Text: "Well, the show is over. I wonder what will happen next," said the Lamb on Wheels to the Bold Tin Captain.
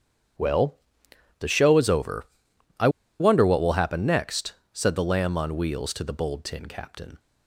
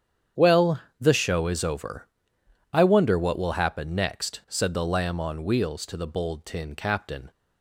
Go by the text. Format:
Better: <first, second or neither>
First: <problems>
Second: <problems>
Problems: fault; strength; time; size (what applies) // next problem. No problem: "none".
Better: second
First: starts louder than the rest; strong; until 2.0 s; 9.5 dB // pauses between "I" and "wonder"; slight; at 2.8 s; 0.31 s long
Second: starts louder than the rest; strong; until 1.5 s; 8.5 dB